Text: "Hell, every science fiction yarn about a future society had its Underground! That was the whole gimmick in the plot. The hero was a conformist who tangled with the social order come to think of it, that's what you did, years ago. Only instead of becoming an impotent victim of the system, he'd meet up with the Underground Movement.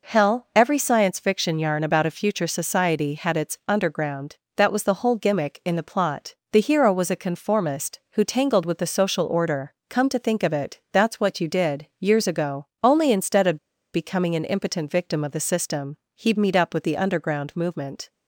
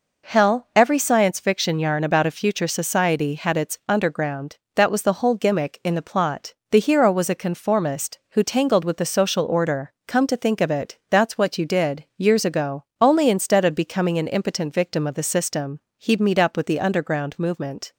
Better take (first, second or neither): second